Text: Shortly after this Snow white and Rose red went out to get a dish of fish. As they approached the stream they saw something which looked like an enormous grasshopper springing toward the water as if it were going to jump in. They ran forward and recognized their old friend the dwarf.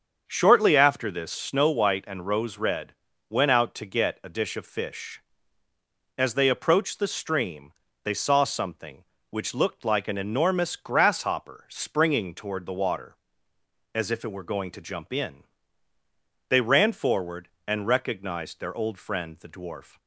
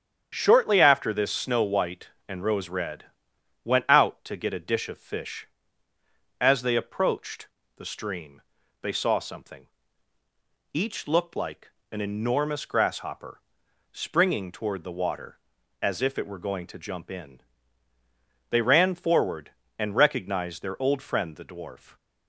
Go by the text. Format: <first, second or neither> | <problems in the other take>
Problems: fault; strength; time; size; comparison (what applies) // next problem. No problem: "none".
first | starts louder than the rest; strong; until 1.3 s; 8.5 dB; also in the first // pauses between "red" and "went"; noticeable; at 3.0 s; 0.60 s long; slight in the first // pauses between "approached" and "the"; slight; at 7.4 s; 0.32 s long // pauses between "stream" and "they"; at 8.4 s; 0.40 s long; slight in the first // says "each" for "which"; at 10.7 s // pauses between "like" and "an"; slight; at 11.6 s; 0.22 s long // pauses between "grasshopper" and "springing"; noticeable; at 13.4 s; 0.50 s long